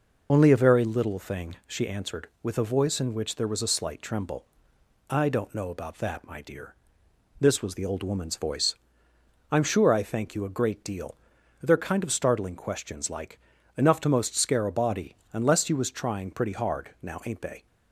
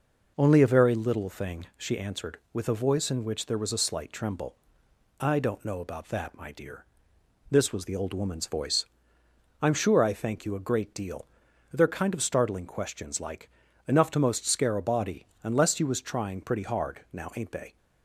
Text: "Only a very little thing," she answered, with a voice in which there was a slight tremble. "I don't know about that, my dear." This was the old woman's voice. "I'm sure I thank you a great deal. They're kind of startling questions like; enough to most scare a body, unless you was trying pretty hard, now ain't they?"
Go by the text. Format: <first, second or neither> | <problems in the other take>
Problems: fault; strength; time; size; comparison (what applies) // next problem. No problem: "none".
second | loses the start of "Only"; at 0.2 s; 45 ms